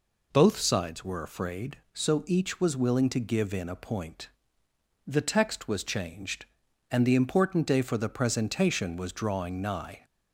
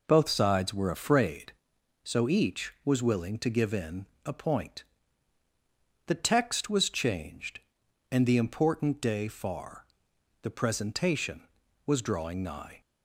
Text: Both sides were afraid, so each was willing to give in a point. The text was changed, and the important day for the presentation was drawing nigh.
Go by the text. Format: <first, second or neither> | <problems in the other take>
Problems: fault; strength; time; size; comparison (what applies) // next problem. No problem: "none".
first | pauses between "in" and "a"; slight; at 4.0 s; 0.20 s long // says "far" for "for"; at 9.2 s